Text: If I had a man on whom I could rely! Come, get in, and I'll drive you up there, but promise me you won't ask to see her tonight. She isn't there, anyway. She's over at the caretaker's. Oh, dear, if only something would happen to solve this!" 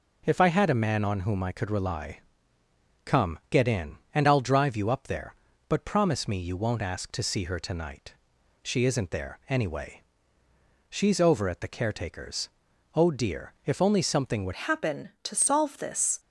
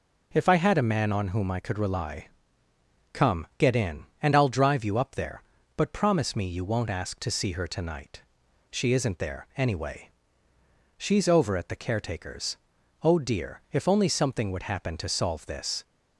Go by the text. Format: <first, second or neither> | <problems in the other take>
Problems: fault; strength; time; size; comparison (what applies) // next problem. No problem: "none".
second | changes voice at "happen"; from 14.5 s on; 1.6 s long